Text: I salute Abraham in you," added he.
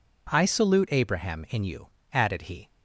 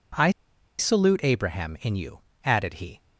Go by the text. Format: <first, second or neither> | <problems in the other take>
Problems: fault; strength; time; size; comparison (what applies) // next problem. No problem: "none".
first | pauses between "I" and "salute"; noticeable; at 0.2 s; 0.49 s long